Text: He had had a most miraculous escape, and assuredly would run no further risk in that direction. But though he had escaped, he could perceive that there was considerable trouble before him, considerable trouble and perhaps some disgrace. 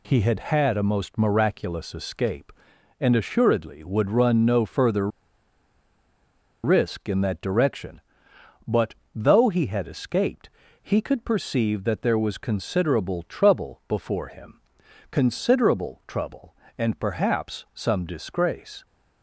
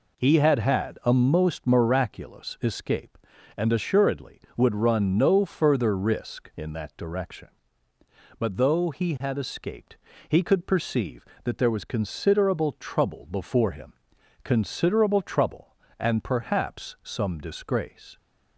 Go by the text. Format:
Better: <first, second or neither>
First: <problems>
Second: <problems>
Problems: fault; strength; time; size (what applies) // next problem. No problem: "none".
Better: second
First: pauses between "further" and "risk"; strong; at 5.0 s; 1.5 s long // pauses between "But" and "though"; slight; at 8.9 s; 0.18 s long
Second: none